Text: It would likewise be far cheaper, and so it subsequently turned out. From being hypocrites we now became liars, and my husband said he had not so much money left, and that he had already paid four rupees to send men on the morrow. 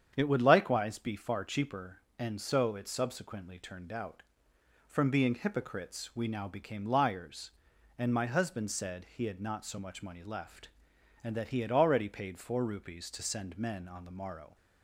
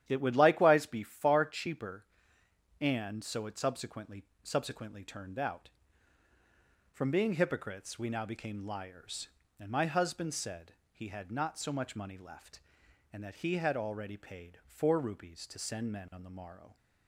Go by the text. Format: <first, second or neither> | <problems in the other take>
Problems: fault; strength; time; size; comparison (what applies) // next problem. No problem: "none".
first | starts louder than the rest; strong; until 1.0 s; 10.5 dB; strong in the first // says "subsequently" twice; at 4.4 s // pauses between "said" and "he"; slight; at 10.7 s; 0.20 s long